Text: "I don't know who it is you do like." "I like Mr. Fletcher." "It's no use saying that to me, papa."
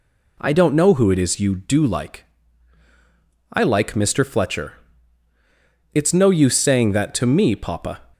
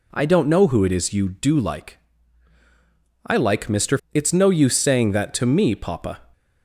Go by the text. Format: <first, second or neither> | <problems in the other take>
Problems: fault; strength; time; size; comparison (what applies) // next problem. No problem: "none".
first | skips "Fletcher"; at 4.0 s